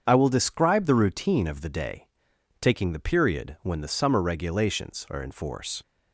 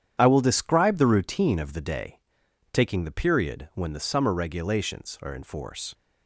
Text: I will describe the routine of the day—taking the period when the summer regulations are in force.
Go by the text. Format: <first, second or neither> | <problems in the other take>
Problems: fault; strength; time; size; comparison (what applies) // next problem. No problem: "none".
first | gets quieter; strong; throughout; 9.5 dB // starts louder than the rest; strong; until 1.2 s; 9.5 dB; strong in the first